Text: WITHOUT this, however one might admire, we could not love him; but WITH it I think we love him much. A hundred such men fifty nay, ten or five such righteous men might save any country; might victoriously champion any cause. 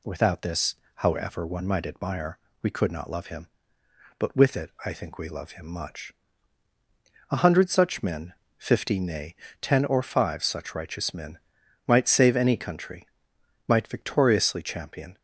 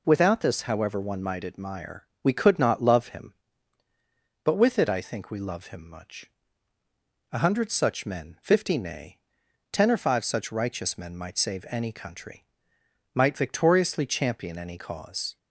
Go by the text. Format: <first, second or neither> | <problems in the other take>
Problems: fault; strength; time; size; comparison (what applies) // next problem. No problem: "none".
second | pauses between "men" and "fifty"; slight; at 8.3 s; 0.24 s long // pauses between "men" and "might"; noticeable; at 11.3 s; 0.46 s long // stops before "any cause"; at 15.1 s